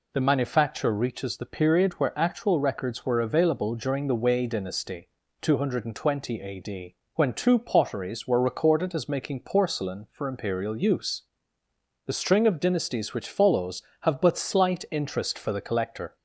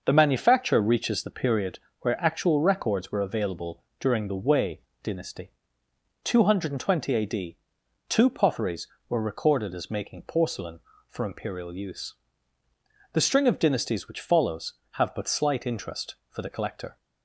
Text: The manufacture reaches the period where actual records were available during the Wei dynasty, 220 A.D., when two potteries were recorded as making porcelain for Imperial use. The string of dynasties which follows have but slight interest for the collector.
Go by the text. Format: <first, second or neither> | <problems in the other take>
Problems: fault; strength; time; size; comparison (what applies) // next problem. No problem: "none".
first | starts louder than the rest; noticeable; until 1.0 s; 6 dB // pauses between "period" and "where"; slight; at 1.7 s; 0.22 s long // pauses between "available" and "during"; slight; at 3.8 s; 0.16 s long // pauses between "Wei" and "dynasty"; slight; at 4.8 s; 0.22 s long // skips "when"; at 7.8 s